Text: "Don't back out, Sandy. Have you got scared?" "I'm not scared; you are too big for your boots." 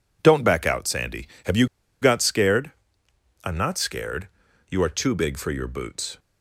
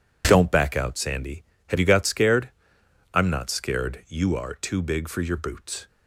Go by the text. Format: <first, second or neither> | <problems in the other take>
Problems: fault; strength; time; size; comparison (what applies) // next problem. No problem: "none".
second | pauses between "you" and "got"; at 1.6 s; 0.36 s long